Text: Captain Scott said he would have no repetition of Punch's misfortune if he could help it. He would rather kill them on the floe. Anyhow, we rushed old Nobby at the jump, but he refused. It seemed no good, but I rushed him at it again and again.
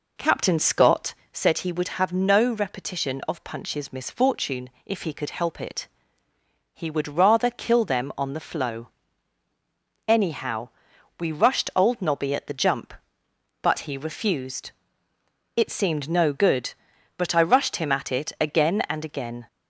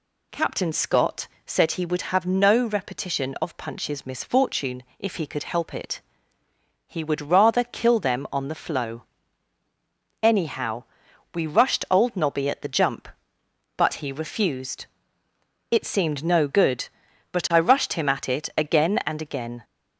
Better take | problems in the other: second | starts louder than the rest; noticeable; until 1.2 s; 4 dB // pauses between "Scott" and "said"; slight; at 1.1 s; 0.20 s long; slight in the second // pauses between "misfortune" and "if"; slight; at 4.7 s; 0.16 s long; slight in the second

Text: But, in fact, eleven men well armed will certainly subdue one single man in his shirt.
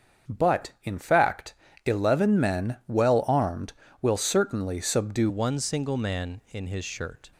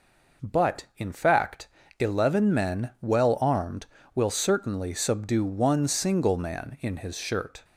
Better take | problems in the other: second | starts louder than the rest; strong; until 1.3 s; 7 dB // changes voice at "one"; from 5.2 s on; 2.1 s long

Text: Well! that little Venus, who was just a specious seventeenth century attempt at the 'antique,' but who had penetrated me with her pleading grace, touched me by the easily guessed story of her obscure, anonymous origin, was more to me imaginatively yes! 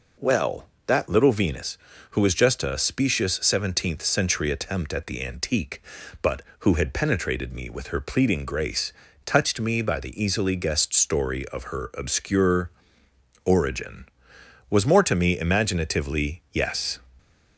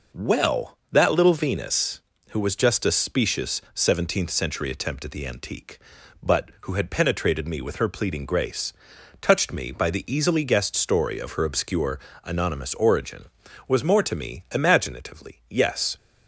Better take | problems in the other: second | skips "anonymous"; at 13.0 s

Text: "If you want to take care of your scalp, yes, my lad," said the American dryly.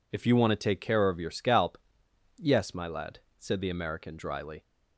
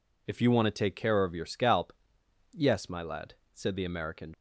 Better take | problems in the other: first | stops before "dryly"; at 4.3 s

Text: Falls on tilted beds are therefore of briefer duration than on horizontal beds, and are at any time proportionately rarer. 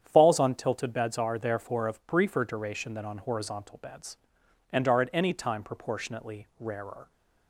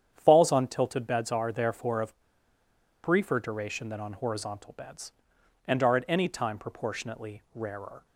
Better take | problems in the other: first | starts louder than the rest; strong; until 1.1 s; 9 dB; strong in the first // pauses between "of" and "briefer"; noticeable; at 2.1 s; 0.84 s long

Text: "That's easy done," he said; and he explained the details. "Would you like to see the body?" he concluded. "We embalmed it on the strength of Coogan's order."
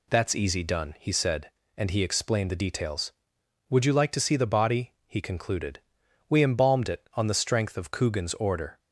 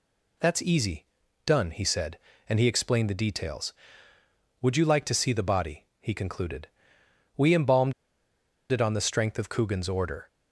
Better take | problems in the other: first | pauses between "easy" and "done"; at 1.0 s; 0.40 s long // pauses between "embalmed" and "it"; noticeable; at 7.9 s; 0.78 s long

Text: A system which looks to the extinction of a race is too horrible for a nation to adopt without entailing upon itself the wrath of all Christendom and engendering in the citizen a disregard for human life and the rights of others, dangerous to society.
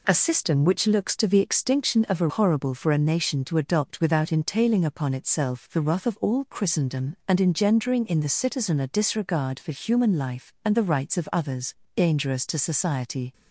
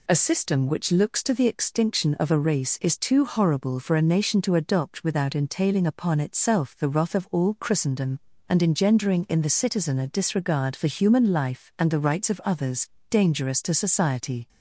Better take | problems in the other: second | skips "race is too"; at 2.2 s

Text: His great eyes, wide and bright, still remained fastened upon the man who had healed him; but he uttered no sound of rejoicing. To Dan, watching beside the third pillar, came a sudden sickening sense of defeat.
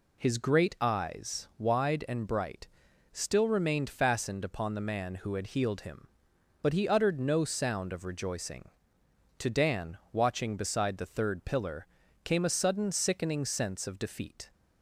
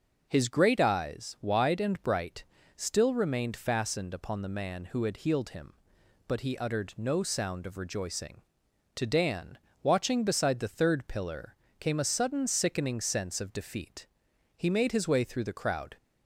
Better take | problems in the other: first | goes on to say "He made his way through the crowd"; from 14.5 s on; 1.4 s long

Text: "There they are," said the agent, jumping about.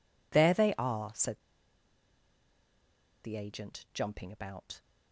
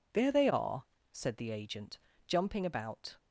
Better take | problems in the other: second | pauses between "said" and "the"; strong; at 1.3 s; 1.8 s long

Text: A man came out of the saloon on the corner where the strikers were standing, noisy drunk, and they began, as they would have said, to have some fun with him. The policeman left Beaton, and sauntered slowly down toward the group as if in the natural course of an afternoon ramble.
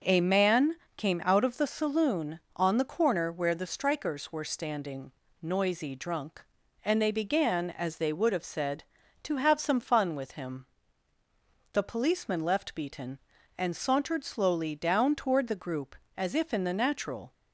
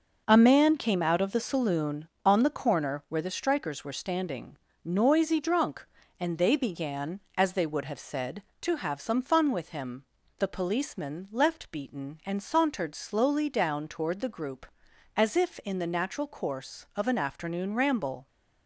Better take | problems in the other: second | pauses between "man" and "came"; slight; at 0.7 s; 0.22 s long // stops before "course of an afternoon ramble"; at 17.3 s

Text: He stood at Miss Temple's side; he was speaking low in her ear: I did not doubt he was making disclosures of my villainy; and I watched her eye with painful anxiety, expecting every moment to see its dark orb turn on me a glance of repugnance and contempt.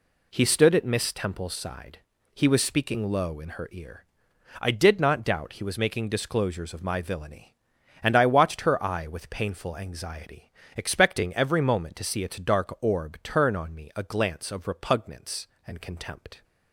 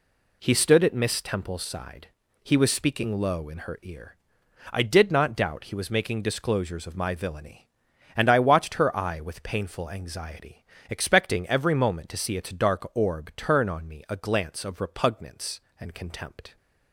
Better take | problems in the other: neither | none

